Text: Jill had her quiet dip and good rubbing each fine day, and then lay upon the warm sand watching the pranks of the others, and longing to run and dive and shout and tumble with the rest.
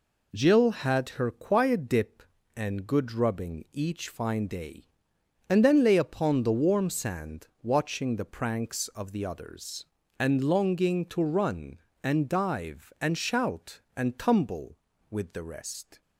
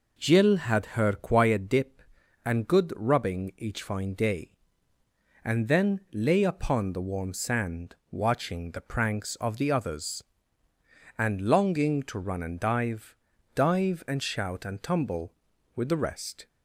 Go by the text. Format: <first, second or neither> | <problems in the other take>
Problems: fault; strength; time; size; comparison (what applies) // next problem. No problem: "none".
first | pauses between "sand" and "watching"; slight; at 7.9 s; 0.16 s long; slight in the first // says "dive" twice; at 13.5 s